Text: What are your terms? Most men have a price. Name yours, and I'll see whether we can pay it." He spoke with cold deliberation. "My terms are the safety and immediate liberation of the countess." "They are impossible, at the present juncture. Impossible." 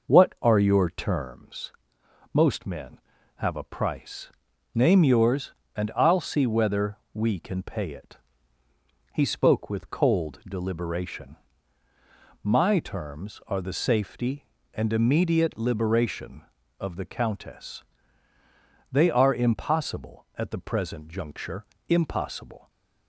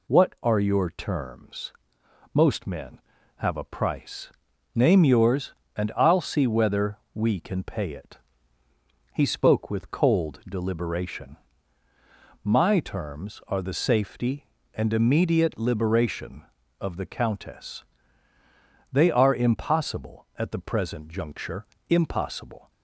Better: second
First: starts louder than the rest; noticeable; until 1.4 s; 5.5 dB // pauses between "whether" and "we"; slight; at 6.9 s; 0.18 s long // stays silent after the last word; slight; from 22.5 s on; 0.5 s long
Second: pauses between "whether" and "we"; slight; at 6.9 s; 0.18 s long

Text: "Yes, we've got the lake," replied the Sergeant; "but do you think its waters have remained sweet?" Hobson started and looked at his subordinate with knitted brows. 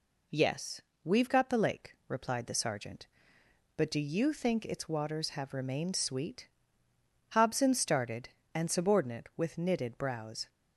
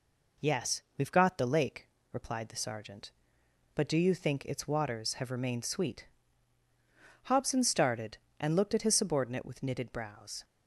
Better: second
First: skips "looked at his"; at 8.7 s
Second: none

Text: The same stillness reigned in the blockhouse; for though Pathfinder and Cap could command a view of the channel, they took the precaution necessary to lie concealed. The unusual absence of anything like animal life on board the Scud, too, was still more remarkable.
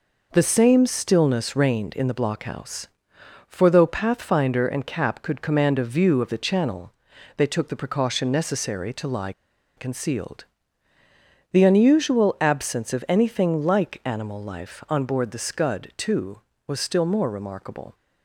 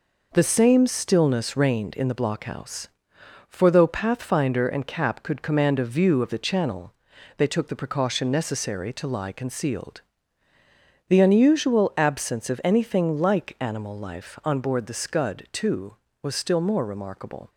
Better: second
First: pauses between "lie" and "concealed"; at 9.3 s; 0.45 s long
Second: none

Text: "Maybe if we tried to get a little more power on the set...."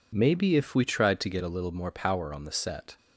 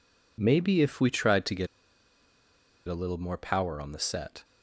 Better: first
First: none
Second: pauses between "get" and "a"; at 1.6 s; 1.2 s long

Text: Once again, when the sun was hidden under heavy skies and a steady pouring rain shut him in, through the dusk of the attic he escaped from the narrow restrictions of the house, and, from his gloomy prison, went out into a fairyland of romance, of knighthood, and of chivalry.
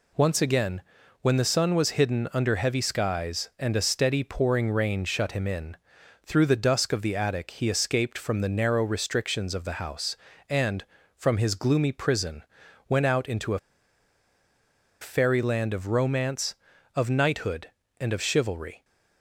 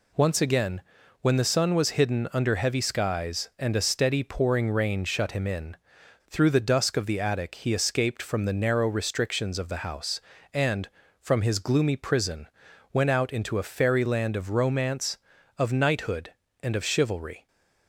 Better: second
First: pauses between "a" and "fairyland"; strong; at 13.5 s; 1.4 s long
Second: none

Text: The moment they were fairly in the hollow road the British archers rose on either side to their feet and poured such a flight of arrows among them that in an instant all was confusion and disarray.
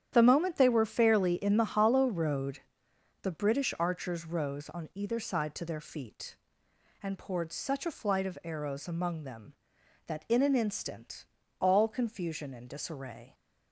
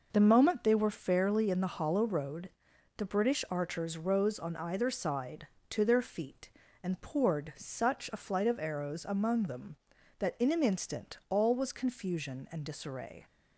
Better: second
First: starts louder than the rest; strong; until 1.1 s; 10 dB // pauses between "road" and "the"; noticeable; at 2.5 s; 0.64 s long // pauses between "instant" and "all"; slight; at 11.2 s; 0.34 s long // skips "was"; at 11.8 s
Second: pauses between "road" and "the"; noticeable; at 2.4 s; 0.48 s long

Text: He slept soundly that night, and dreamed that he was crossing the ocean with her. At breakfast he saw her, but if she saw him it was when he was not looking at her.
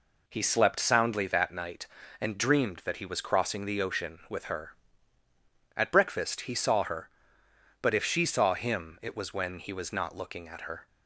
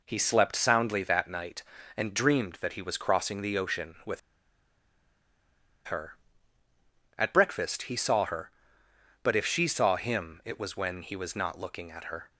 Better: first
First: none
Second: pauses between "with" and "her"; strong; at 4.1 s; 1.6 s long

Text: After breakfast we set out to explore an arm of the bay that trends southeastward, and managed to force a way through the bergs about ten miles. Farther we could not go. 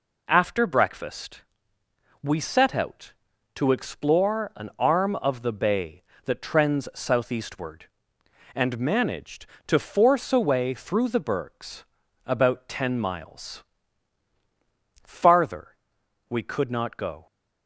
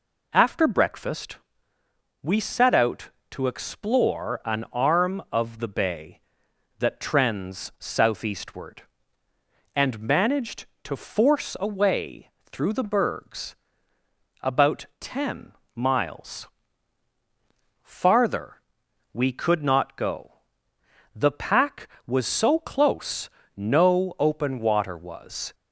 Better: first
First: pauses between "breakfast" and "we"; noticeable; at 1.4 s; 0.80 s long // pauses between "bergs" and "about"; at 11.8 s; 0.42 s long // pauses between "Farther" and "we"; noticeable; at 15.7 s; 0.52 s long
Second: pauses between "breakfast" and "we"; noticeable; at 1.3 s; 0.84 s long // pauses between "way" and "through"; slight; at 12.2 s; 0.20 s long // pauses between "bergs" and "about"; noticeable; at 13.5 s; 0.88 s long // pauses between "ten" and "miles"; slight; at 15.5 s; 0.24 s long // pauses between "Farther" and "we"; noticeable; at 18.5 s; 0.58 s long // goes on to say "The pack was so close no open water was"; strong; from 21.1 s on; 4.4 s long

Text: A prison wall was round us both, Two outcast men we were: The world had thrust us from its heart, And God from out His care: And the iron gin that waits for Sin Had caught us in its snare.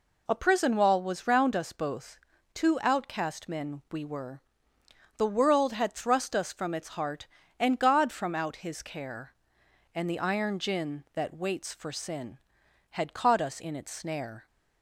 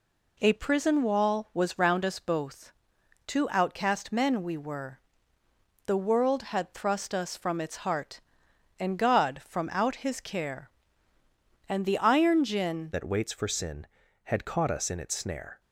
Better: first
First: none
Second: changes voice at "that"; from 12.9 s on; 2.7 s long

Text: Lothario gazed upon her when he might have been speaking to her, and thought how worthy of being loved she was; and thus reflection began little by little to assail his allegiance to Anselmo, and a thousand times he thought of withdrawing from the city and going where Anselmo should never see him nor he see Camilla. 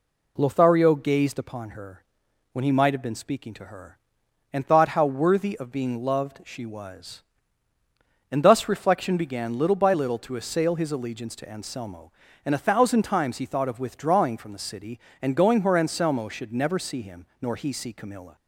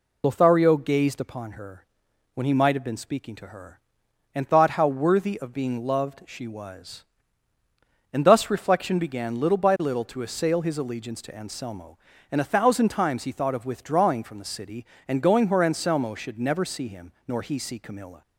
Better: first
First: pauses between "her" and "when"; noticeable; at 2.0 s; 0.50 s long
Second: loses the start of "Lothario"; at 0.2 s; 50 ms // pauses between "her" and "when"; noticeable; at 1.8 s; 0.50 s long

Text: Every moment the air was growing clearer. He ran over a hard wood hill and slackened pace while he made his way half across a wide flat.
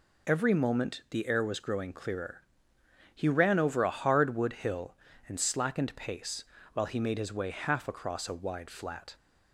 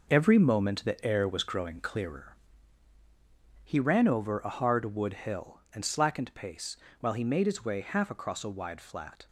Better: first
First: pauses between "pace" and "while"; slight; at 6.4 s; 0.30 s long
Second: gets quieter; strong; throughout; 7.5 dB // pauses between "pace" and "while"; slight; at 6.7 s; 0.24 s long

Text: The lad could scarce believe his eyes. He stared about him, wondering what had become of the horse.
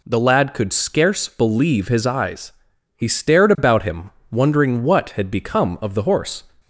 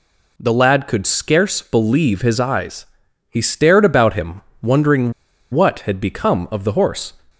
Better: first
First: none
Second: pauses between "wondering" and "what"; at 5.1 s; 0.39 s long

